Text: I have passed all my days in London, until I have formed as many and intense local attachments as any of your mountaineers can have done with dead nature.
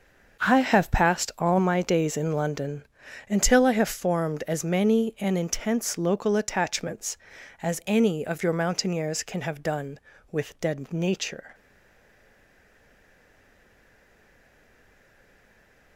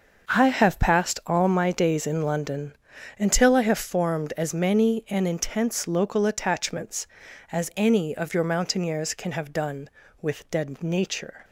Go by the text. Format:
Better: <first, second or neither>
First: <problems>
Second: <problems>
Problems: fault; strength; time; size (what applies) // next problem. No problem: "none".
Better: second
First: starts louder than the rest; until 1.5 s; 6.5 dB // stays silent after the last word; strong; from 11.5 s on; 4.4 s long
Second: starts louder than the rest; until 1.4 s; 6.5 dB